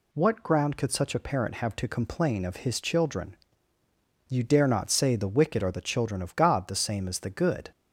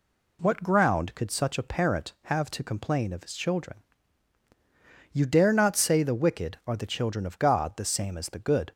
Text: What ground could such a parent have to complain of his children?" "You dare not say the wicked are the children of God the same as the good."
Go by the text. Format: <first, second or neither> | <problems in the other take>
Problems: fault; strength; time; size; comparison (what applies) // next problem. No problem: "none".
neither | none